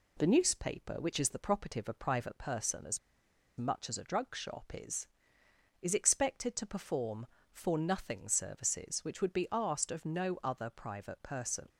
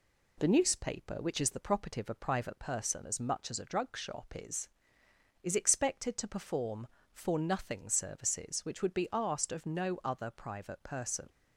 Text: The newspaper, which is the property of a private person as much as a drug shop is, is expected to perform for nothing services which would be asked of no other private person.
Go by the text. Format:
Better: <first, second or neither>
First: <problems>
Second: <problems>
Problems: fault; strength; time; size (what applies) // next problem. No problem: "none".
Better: second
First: pauses between "as" and "much"; noticeable; at 2.9 s; 0.59 s long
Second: none